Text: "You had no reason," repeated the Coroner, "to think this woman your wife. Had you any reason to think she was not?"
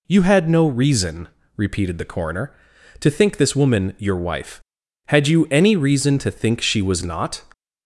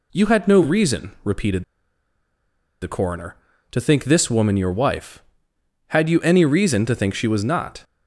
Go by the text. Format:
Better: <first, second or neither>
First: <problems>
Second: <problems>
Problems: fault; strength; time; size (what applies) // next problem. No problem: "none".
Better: first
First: none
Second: pauses between "repeated" and "the"; at 1.6 s; 1.1 s long